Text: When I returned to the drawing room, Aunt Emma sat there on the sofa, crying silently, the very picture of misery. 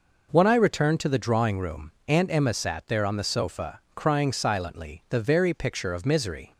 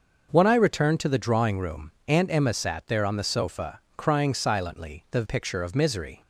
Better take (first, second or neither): first